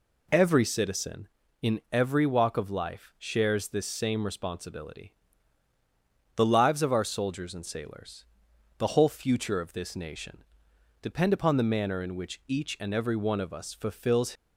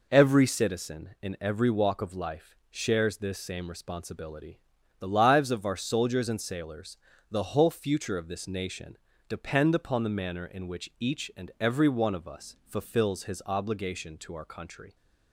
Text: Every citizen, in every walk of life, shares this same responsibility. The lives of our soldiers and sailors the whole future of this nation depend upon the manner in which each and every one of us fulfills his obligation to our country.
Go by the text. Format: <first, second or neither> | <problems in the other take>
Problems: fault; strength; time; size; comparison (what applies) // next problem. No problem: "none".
second | pauses between "sailors" and "the"; noticeable; at 8.2 s; 0.52 s long; slight in the second // pauses between "nation" and "depend"; noticeable; at 10.4 s; 0.60 s long; slight in the second // stops before "his obligation to our country"; at 14.3 s